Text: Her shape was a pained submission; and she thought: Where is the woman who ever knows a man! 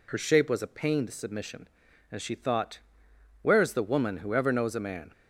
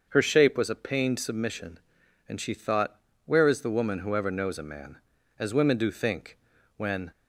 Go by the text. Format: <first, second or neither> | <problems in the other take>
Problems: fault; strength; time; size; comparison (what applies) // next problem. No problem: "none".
first | starts louder than the rest; until 1.1 s; 6.5 dB // goes on to say "as women do think when"; strong; from 5.3 s on; 1.7 s long